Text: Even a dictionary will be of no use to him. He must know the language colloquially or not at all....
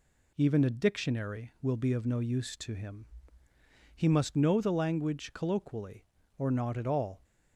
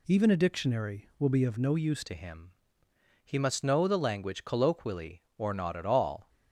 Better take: first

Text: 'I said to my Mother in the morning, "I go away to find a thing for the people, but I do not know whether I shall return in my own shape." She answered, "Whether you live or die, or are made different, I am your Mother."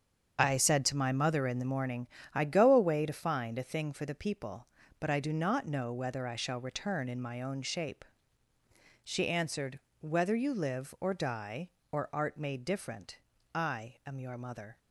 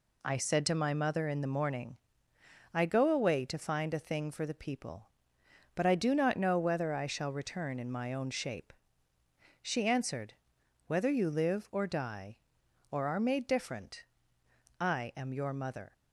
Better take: second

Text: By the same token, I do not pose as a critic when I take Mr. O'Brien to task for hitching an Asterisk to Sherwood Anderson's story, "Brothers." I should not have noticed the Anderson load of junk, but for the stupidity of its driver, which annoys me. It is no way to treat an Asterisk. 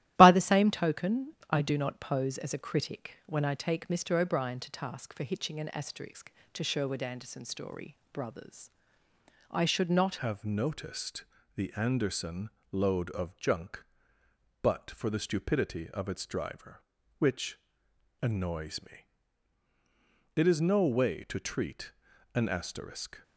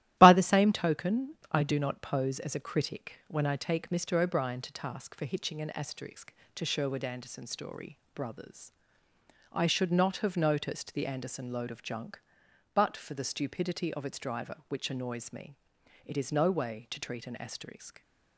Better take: second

